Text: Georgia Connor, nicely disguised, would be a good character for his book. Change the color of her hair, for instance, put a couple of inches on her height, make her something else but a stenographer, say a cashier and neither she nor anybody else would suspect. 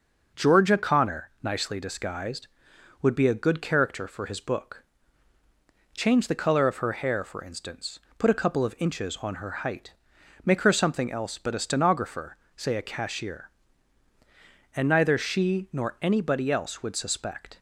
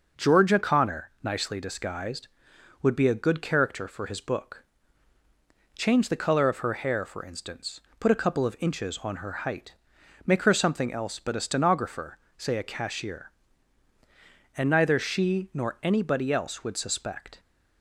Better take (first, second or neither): neither